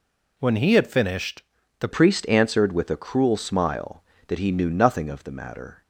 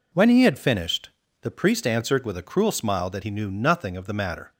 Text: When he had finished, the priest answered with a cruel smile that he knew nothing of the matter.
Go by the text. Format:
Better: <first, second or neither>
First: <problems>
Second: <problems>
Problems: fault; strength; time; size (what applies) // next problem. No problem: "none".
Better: second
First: changes voice at "priest"; from 1.9 s on; 3.9 s long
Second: none